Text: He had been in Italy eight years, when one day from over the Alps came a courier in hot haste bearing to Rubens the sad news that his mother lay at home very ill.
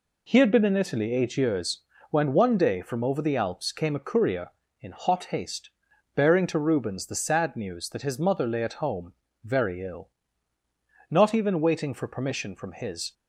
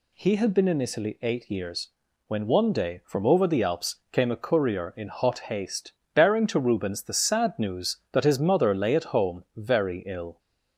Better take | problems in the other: second | pauses between "haste" and "bearing"; noticeable; at 5.6 s; 0.46 s long; slight in the second // pauses between "home" and "very"; slight; at 9.1 s; 0.32 s long // goes on to say "Not even waiting for permission from his"; strong; from 11.0 s on; 2.0 s long

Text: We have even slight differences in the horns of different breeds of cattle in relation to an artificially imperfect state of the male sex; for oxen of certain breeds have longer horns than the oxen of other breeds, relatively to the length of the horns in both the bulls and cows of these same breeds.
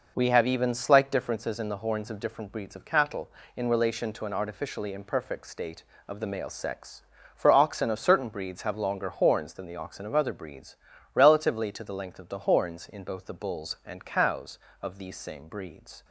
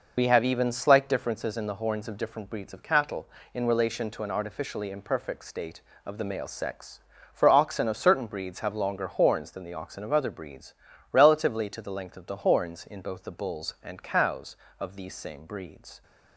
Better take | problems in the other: first | loses the start of "We"; at 0.1 s; 35 ms

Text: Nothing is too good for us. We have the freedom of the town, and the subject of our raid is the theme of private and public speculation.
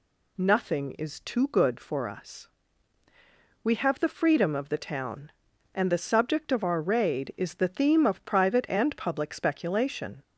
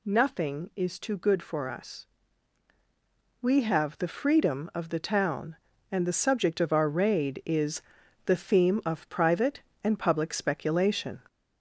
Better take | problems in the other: first | gets louder; noticeable; throughout; 4 dB // pauses between "is" and "the"; at 7.8 s; 0.44 s long

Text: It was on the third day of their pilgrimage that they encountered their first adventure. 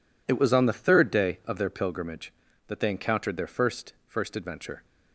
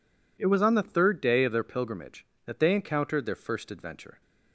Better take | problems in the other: second | says "first" twice; at 4.0 s

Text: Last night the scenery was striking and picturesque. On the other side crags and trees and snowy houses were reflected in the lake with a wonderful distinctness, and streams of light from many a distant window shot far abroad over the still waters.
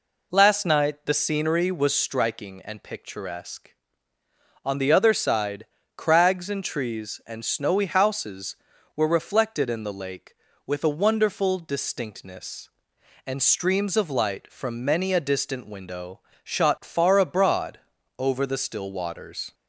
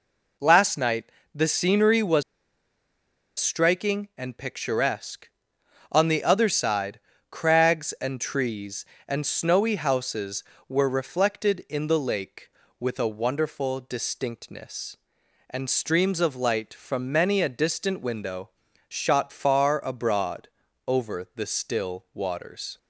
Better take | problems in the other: first | pauses between "night" and "the"; slight; at 1.0 s; 0.28 s long // pauses between "was" and "striking"; at 2.2 s; 1.1 s long // pauses between "side" and "crags"; slight; at 6.9 s; 0.30 s long; slight in the first // pauses between "window" and "shot"; at 18.4 s; 0.38 s long; slight in the first // pauses between "abroad" and "over"; at 20.4 s; 0.38 s long; also in the first

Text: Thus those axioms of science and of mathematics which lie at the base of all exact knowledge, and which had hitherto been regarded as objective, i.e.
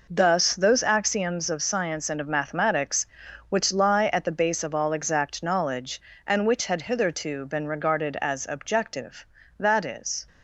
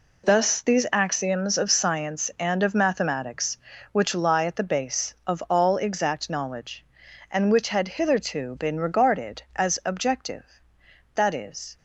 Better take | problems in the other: first | says "these" for "those"; at 0.6 s

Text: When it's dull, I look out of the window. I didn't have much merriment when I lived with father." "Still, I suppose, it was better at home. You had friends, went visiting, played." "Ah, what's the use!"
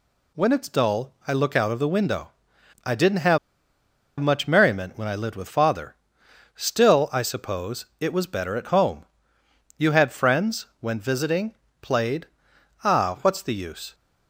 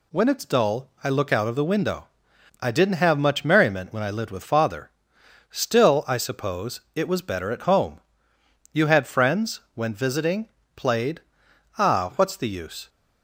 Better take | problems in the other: second | pauses between "have" and "much"; noticeable; at 3.3 s; 0.82 s long

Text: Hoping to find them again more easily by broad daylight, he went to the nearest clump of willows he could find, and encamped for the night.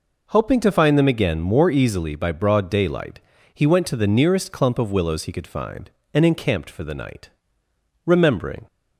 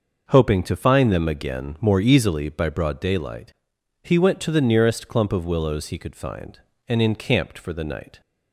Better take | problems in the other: second | goes on to say "Remembering"; from 8.0 s on; 0.60 s long

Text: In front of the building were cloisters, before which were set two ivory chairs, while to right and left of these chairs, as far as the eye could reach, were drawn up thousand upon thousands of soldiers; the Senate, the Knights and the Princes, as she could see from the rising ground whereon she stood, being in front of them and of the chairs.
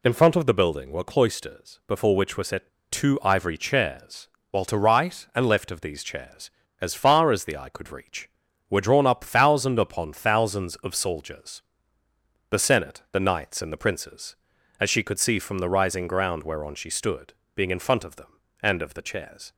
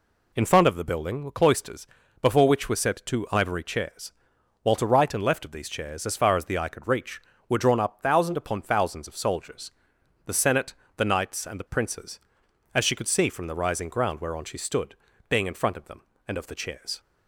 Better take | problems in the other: second | pauses between "set" and "two"; slight; at 2.6 s; 0.21 s long

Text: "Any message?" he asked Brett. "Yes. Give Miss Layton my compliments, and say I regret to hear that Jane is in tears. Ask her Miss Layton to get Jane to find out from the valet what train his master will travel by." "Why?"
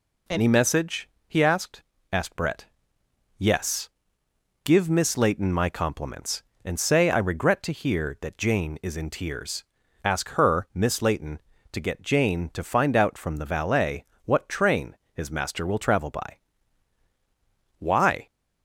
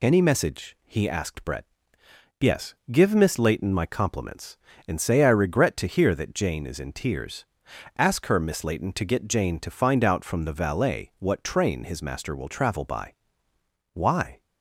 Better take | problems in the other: second | says "asked" twice; at 2.1 s // pauses between "valet" and "what"; slight; at 14.0 s; 0.20 s long // pauses between "train" and "his"; slight; at 14.9 s; 0.16 s long

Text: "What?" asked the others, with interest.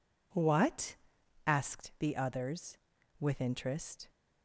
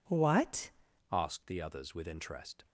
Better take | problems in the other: first | changes voice at "asked"; from 1.1 s on; 1.5 s long

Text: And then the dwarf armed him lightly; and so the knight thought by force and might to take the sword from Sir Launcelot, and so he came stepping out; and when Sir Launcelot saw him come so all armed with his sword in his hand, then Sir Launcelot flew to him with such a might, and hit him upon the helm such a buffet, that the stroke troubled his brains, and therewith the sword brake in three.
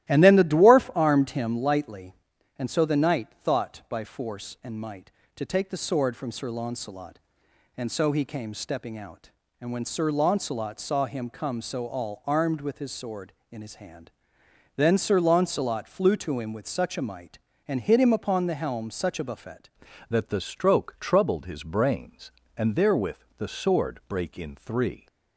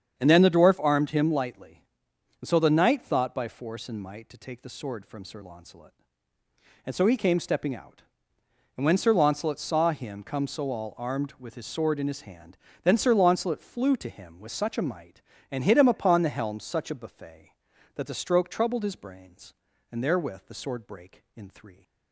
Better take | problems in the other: second | starts louder than the rest; strong; until 1.1 s; 14.5 dB; strong in the second // pauses between "knight" and "thought"; slight; at 3.2 s; 0.16 s long // changes voice at "that"; from 20.0 s on; 5.0 s long // pauses between "therewith" and "the"; slight; at 23.1 s; 0.18 s long

